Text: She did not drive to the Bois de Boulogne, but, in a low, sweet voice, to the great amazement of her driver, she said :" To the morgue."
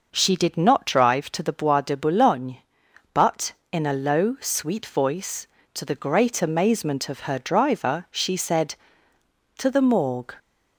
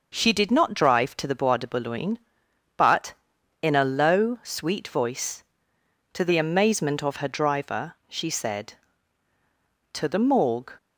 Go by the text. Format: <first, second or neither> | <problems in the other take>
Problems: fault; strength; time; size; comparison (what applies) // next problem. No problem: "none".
first | starts louder than the rest; until 1.1 s; 6.5 dB; noticeable in the first // skips "great"; at 6.3 s